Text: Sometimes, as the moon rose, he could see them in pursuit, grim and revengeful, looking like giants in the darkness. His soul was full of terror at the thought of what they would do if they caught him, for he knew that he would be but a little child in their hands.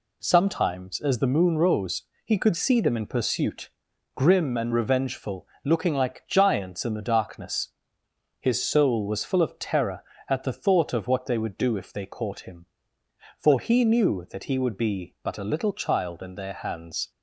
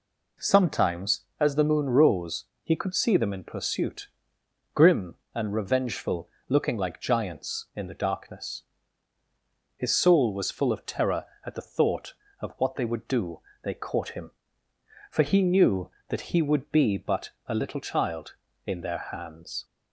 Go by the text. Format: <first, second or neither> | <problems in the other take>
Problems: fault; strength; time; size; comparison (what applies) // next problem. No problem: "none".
first | skips "if"; at 13.5 s // pauses between "but" and "a"; slight; at 17.3 s; 0.16 s long